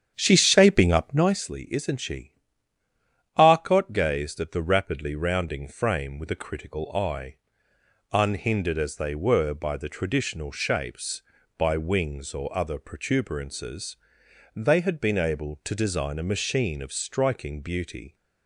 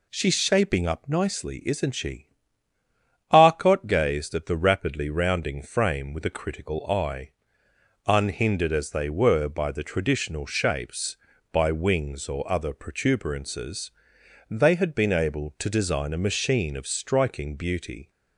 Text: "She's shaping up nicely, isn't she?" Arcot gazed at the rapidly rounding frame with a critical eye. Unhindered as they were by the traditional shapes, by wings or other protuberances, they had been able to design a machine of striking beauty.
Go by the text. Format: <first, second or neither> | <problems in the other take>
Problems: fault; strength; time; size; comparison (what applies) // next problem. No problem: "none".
second | starts louder than the rest; strong; until 1.4 s; 9 dB